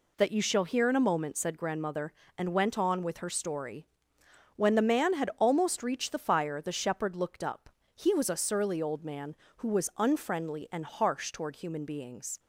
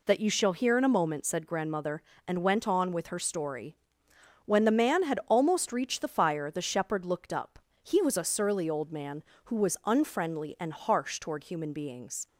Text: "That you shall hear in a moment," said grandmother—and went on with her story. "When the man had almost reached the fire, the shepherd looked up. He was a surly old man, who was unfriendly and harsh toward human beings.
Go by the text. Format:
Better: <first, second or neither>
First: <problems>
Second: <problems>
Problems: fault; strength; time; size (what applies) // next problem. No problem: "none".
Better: neither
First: none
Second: none